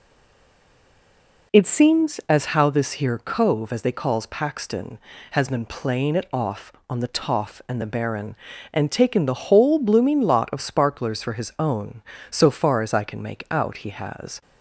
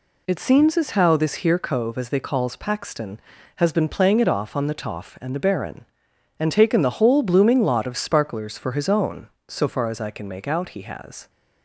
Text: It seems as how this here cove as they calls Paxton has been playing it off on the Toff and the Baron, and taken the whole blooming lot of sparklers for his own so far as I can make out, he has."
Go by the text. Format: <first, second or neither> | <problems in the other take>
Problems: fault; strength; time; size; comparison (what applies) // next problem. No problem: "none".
second | stays silent before the first word; noticeable; until 1.5 s; 1.5 s long